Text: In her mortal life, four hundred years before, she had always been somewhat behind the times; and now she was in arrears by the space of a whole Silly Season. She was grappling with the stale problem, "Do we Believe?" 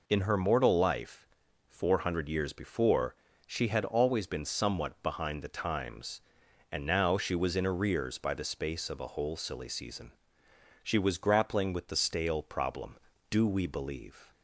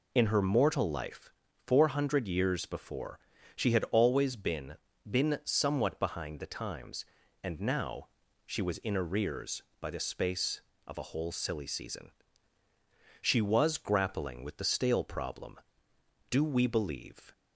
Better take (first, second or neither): first